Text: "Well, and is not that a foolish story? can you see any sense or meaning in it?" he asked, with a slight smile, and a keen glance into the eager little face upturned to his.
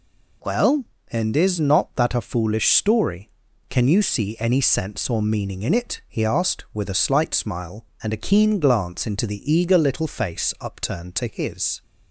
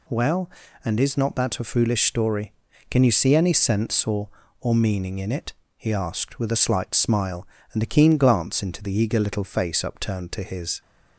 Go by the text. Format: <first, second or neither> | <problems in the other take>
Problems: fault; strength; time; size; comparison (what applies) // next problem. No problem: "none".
first | says "or" twice; at 4.6 s